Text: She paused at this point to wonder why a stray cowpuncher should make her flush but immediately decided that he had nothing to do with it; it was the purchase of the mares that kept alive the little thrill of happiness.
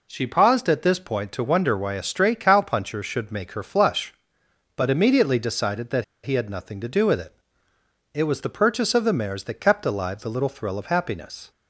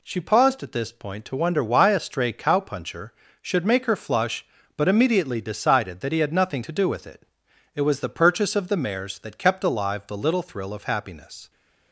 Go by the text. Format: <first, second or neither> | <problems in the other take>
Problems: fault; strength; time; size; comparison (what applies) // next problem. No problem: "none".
second | pauses between "that" and "he"; slight; at 6.0 s; 0.19 s long